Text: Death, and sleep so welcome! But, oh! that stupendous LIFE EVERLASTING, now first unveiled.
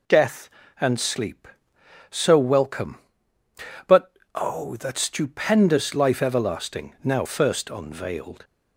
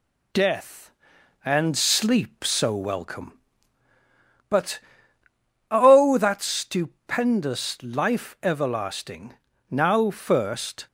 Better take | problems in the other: first | stops before "unveiled"; at 10.8 s

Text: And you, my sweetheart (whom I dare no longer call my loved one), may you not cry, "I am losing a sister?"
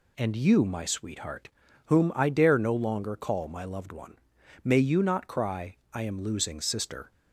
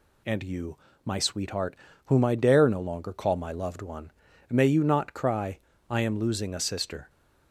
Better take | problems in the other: second | skips "a"; at 6.6 s

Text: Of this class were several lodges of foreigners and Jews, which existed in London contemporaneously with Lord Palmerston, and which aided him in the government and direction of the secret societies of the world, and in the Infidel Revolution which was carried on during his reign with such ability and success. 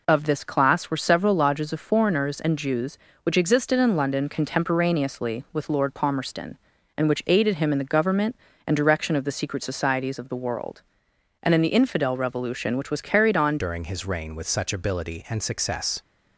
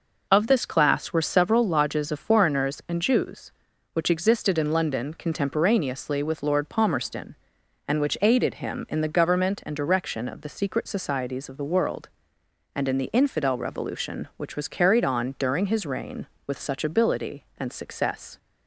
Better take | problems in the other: second | changes voice at "during"; from 13.5 s on; 2.5 s long

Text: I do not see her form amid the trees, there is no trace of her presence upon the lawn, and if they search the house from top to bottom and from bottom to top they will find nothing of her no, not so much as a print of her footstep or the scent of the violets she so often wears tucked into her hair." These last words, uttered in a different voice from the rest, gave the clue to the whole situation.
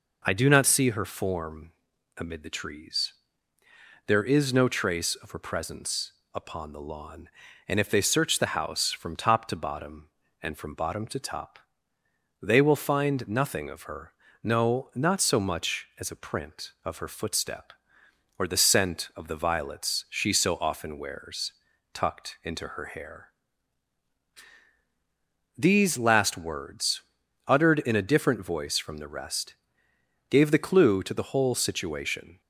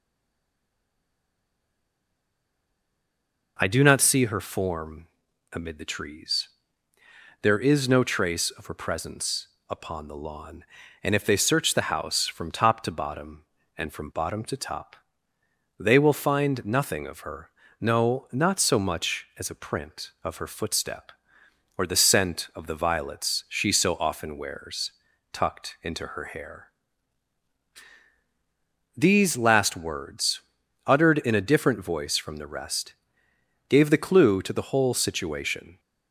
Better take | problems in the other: first | stays silent before the first word; strong; until 3.5 s; 3.5 s long // pauses between "form" and "amid"; at 5.0 s; 0.44 s long; also in the first // pauses between "presence" and "upon"; slight; at 9.4 s; 0.22 s long; slight in the first // pauses between "top" and "they"; noticeable; at 14.9 s; 0.86 s long; noticeable in the first // pauses between "her" and "no"; slight; at 17.4 s; 0.32 s long; slight in the first // pauses between "wears" and "tucked"; at 24.9 s; 0.40 s long; also in the first

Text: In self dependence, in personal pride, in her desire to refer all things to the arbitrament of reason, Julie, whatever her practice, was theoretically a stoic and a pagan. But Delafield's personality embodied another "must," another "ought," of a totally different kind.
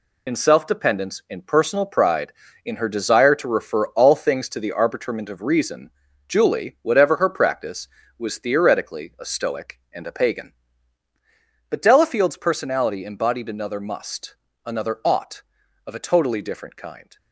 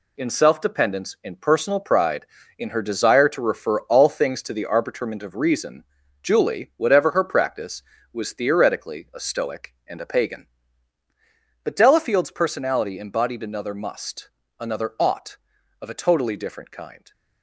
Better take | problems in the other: second | loses the start of "In"; at 0.2 s; 45 ms

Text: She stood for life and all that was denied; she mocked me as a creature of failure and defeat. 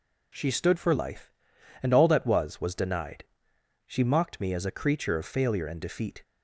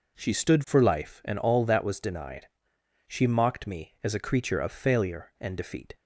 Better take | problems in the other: second | says "was" twice; at 2.6 s

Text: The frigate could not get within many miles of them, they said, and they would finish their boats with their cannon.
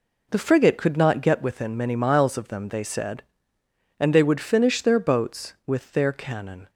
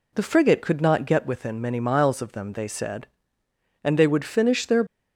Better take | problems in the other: first | stops before "boats with their cannon"; at 4.8 s

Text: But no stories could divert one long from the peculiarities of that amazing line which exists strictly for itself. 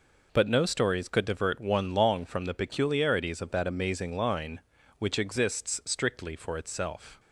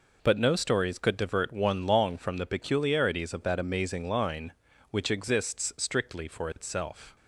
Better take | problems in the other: neither | none

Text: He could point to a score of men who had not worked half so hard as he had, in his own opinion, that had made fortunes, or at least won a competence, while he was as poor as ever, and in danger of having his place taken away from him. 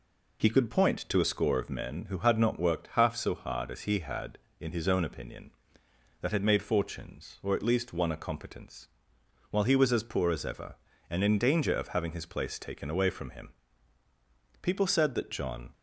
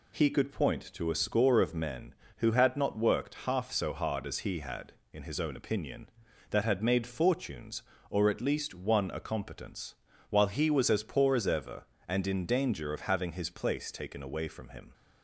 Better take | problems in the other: second | goes on to say "People said that John"; noticeable; from 14.6 s on; 1.1 s long

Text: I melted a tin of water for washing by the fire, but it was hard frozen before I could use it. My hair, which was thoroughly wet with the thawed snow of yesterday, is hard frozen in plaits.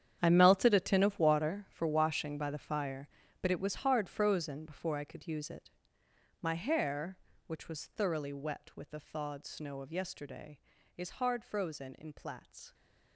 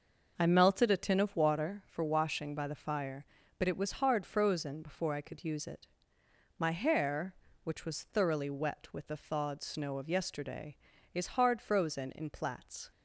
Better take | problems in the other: second | gets quieter; strong; throughout; 15 dB

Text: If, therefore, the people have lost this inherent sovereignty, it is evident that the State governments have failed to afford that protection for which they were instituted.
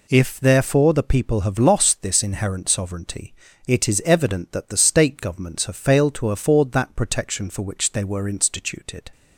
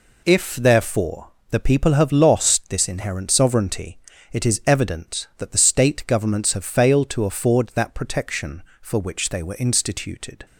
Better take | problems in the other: neither | none

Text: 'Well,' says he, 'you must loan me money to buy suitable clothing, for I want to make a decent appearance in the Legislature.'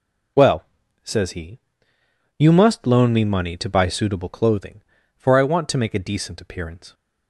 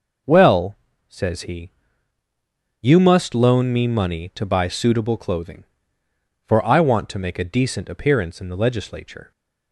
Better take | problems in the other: second | stops before "in the Legislature"; at 6.9 s

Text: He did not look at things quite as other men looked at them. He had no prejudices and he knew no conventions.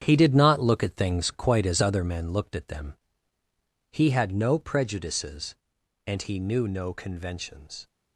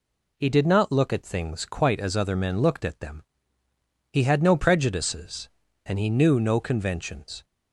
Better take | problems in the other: second | gets quieter; strong; throughout; 9.5 dB

